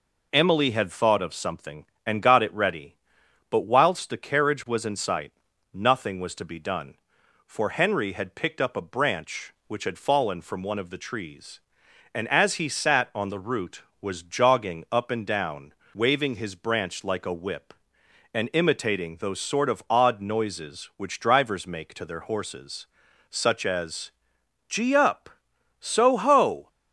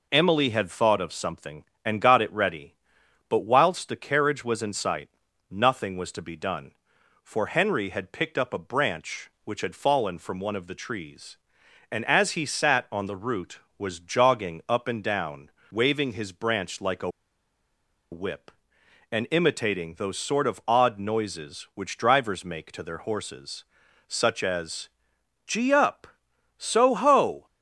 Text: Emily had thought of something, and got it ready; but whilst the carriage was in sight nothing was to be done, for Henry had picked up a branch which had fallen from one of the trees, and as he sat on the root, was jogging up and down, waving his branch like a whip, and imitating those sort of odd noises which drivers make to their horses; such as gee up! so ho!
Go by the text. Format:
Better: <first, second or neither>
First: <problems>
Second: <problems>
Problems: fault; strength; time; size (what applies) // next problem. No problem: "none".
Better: first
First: pauses between "sight" and "nothing"; at 5.3 s; 0.42 s long // pauses between "as" and "gee"; noticeable; at 24.1 s; 0.58 s long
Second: pauses between "sight" and "nothing"; at 5.0 s; 0.42 s long // pauses between "a" and "whip"; at 17.0 s; 1.0 s long // pauses between "as" and "gee"; noticeable; at 24.8 s; 0.58 s long